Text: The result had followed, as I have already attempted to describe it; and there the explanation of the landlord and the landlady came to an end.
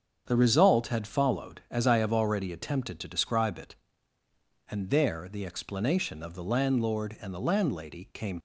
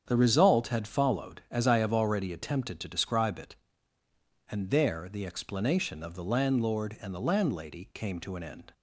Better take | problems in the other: second | starts louder than the rest; strong; until 1.2 s; 7 dB; strong in the second // stops before "to an end"; at 8.3 s

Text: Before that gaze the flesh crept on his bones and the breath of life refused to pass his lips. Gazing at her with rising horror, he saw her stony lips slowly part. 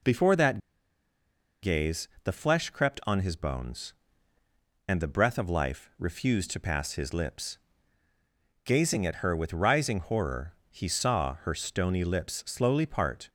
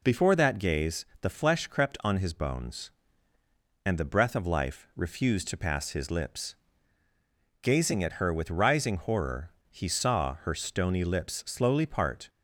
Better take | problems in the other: second | pauses between "that" and "gaze"; at 0.5 s; 1.0 s long // pauses between "gaze" and "the"; slight; at 2.0 s; 0.16 s long; slight in the second

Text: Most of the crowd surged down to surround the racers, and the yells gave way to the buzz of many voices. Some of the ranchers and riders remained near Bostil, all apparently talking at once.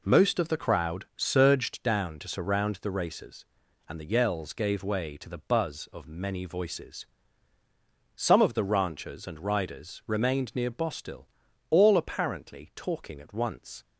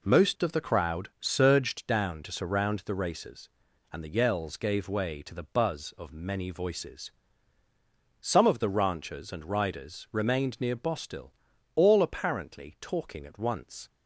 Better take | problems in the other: neither | none

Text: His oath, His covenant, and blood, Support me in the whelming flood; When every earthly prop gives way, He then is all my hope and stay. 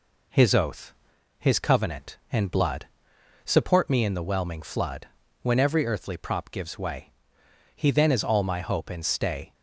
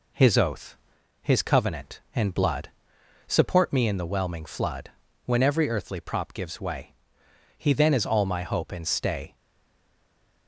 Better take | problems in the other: first | stays silent after the last word; noticeable; from 9.3 s on; 1.1 s long

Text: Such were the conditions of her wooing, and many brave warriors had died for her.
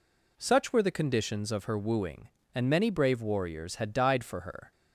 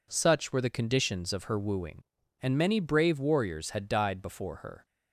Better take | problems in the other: first | says "before" for "for"; at 4.2 s

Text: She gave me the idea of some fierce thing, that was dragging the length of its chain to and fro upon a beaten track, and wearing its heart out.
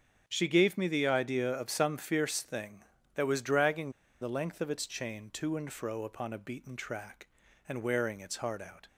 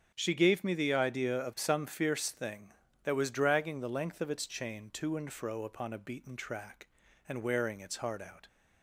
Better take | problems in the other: second | starts louder than the rest; until 1.2 s; 7 dB; strong in the second // pauses between "dragging" and "the"; slight; at 3.9 s; 0.29 s long

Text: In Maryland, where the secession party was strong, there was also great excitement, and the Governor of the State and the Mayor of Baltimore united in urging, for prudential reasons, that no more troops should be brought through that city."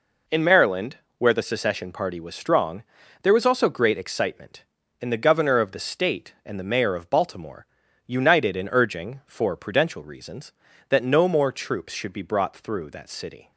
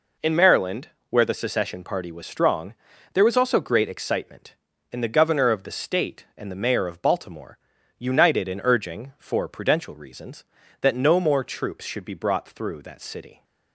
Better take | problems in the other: neither | pauses between "Baltimore" and "united"; the same in both

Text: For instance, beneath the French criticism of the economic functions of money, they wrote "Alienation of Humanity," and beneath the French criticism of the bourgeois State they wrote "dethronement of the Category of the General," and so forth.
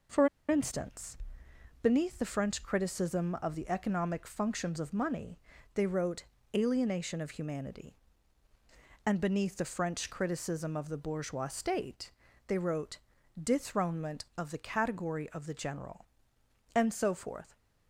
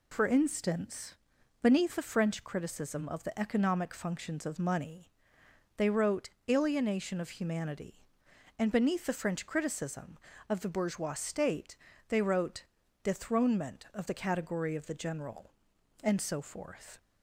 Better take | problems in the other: second | pauses between "For" and "instance"; slight; at 0.2 s; 0.22 s long // pauses between "wrote" and "Alienation"; slight; at 6.2 s; 0.32 s long; slight in the second // pauses between "State" and "they"; slight; at 12.1 s; 0.34 s long; slight in the second // pauses between "wrote" and "dethronement"; at 12.9 s; 0.44 s long; also in the second

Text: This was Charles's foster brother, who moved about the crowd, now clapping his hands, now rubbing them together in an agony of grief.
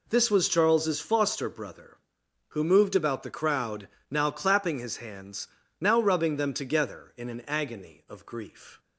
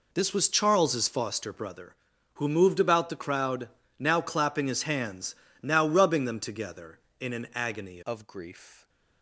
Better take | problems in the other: first | changes voice at "of"; from 8.0 s on; 0.8 s long

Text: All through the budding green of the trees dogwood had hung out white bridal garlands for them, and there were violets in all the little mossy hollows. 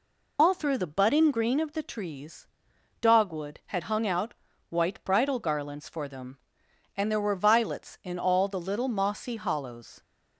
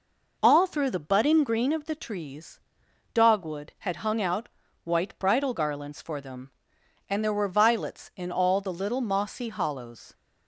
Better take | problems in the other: second | loses the start of "All"; at 0.3 s; 125 ms // pauses between "trees" and "dogwood"; noticeable; at 2.4 s; 0.52 s long; noticeable in the second // pauses between "out" and "white"; slight; at 4.3 s; 0.36 s long; slight in the second

